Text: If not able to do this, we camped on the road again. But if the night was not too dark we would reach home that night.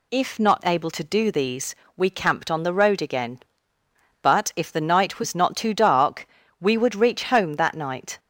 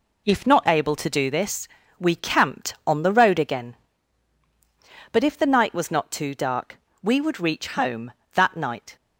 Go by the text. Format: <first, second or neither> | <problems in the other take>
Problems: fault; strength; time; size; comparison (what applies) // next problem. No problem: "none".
second | says "these" for "this"; at 1.3 s // pauses between "dark" and "we"; slight; at 6.2 s; 0.32 s long; slight in the second